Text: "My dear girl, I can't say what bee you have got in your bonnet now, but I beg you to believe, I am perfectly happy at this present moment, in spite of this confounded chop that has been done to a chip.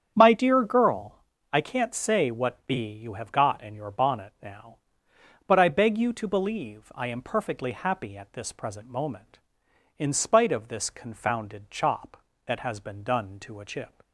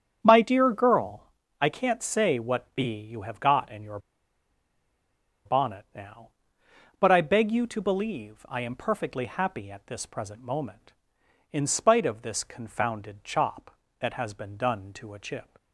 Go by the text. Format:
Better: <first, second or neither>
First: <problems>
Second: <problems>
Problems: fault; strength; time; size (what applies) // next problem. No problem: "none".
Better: first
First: starts louder than the rest; strong; until 1.1 s; 8 dB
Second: starts louder than the rest; strong; until 1.2 s; 8 dB // pauses between "your" and "bonnet"; strong; at 3.9 s; 1.4 s long